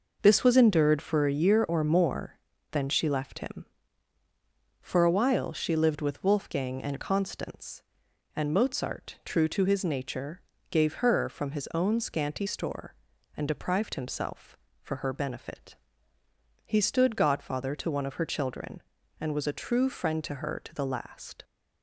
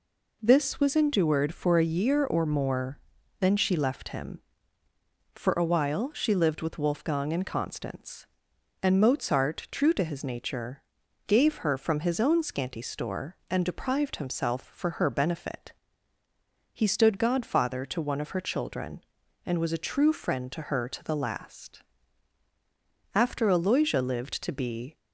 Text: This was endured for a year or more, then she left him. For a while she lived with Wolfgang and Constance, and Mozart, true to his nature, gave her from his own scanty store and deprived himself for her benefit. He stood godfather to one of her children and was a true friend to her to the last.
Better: first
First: none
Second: goes on to say "After Aloysia lived to be"; strong; from 23.1 s on; 1.8 s long

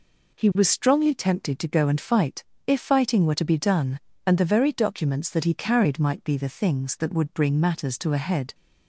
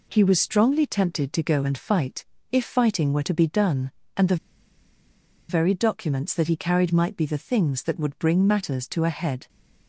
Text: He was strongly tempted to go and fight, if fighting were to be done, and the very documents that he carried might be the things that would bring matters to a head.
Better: first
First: none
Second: pauses between "the" and "very"; at 4.3 s; 1.1 s long

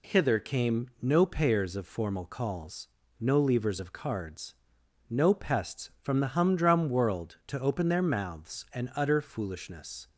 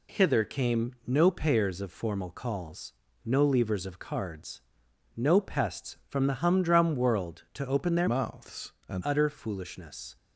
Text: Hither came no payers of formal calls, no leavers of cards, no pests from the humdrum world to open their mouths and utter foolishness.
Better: first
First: none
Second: changes voice from "mouths" to "and"; from 8.0 to 9.0 s; 1.0 s long

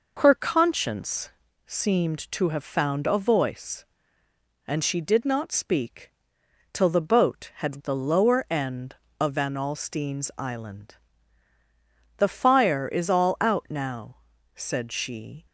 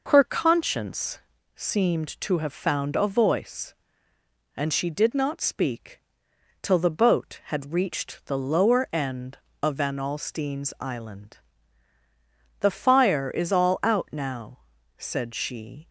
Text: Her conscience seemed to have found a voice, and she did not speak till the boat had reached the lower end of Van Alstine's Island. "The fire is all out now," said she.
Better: second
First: pauses between "conscience" and "seemed"; at 1.2 s; 0.38 s long // pauses between "speak" and "till"; noticeable; at 6.0 s; 0.64 s long // skips "reached"; at 7.8 s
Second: pauses between "conscience" and "seemed"; at 1.1 s; 0.38 s long // pauses between "speak" and "till"; noticeable; at 5.9 s; 0.64 s long

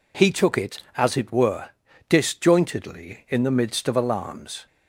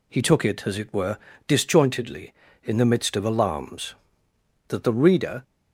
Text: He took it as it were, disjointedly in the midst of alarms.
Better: first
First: none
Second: goes on to say "That the reader"; noticeable; from 4.6 s on; 0.74 s long

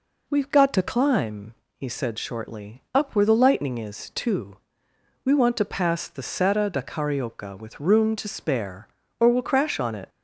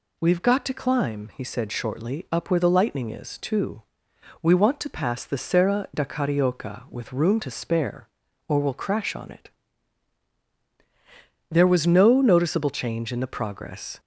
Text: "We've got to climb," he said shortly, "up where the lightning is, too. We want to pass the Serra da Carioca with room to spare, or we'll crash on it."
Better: first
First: none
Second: goes on to say "There was no noticeable change in the progress"; strong; from 11.5 s on; 2.4 s long

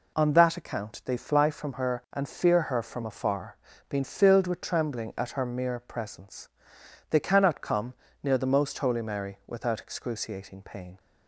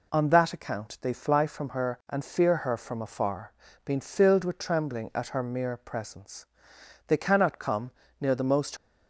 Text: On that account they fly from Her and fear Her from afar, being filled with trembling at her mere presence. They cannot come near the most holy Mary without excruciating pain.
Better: first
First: pauses between "come" and "near"; slight; at 7.9 s; 0.30 s long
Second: pauses between "come" and "near"; slight; at 7.9 s; 0.30 s long // stops before "holy Mary without excruciating pain"; at 8.7 s

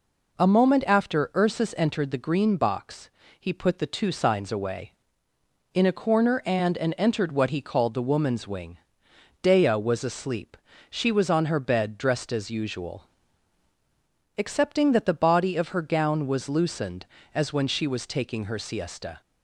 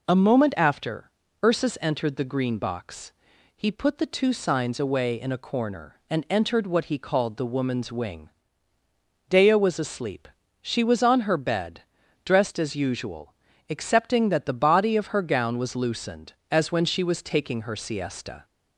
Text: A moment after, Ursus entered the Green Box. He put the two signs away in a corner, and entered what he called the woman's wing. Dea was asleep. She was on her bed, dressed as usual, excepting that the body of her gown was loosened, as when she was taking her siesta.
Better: second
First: says "and" twice; at 6.7 s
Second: none

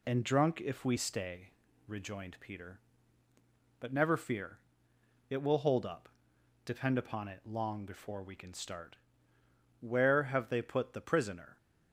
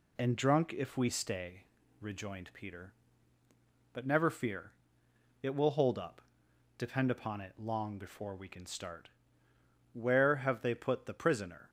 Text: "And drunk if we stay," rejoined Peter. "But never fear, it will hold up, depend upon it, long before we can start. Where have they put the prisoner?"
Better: neither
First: none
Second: none

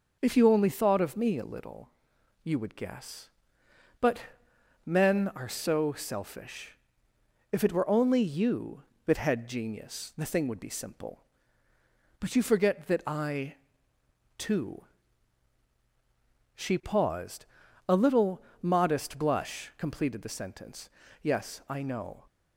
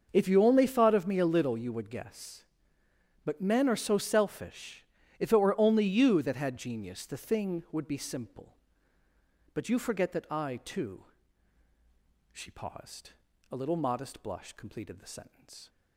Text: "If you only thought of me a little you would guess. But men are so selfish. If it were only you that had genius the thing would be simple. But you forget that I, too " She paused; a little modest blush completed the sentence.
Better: second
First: starts louder than the rest; until 1.2 s; 6.5 dB // pauses between "little" and "you"; noticeable; at 1.9 s; 0.52 s long // pauses between "But" and "men"; noticeable; at 4.2 s; 0.66 s long // pauses between "little" and "modest"; slight; at 18.4 s; 0.18 s long // goes on to say "Yes I know"; noticeable; from 21.2 s on; 1.0 s long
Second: starts louder than the rest; until 1.1 s; 6.5 dB

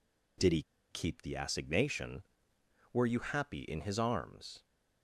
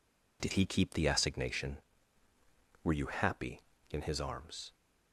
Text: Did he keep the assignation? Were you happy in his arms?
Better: second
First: pauses between "he" and "keep"; slight; at 0.6 s; 0.29 s long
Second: none

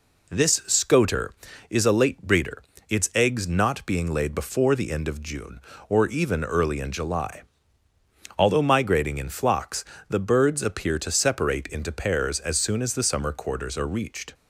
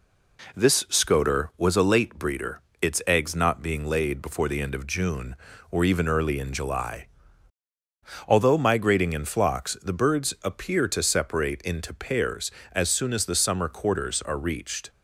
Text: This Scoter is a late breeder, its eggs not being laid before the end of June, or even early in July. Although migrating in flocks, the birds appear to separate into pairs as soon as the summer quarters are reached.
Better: first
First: none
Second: says "was" for "is"; at 1.5 s

